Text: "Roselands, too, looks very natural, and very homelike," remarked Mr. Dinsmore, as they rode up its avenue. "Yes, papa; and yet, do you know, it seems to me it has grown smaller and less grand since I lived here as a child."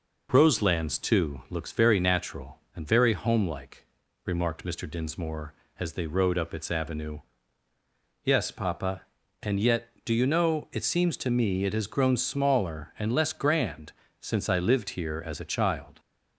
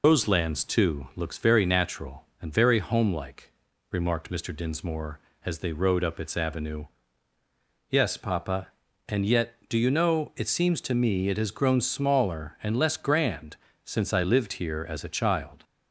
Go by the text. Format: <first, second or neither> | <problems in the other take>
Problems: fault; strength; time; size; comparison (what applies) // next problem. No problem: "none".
first | loses the start of "Roselands"; at 0.0 s; 90 ms // pauses between "grand" and "since"; slight; at 13.5 s; 0.30 s long; slight in the first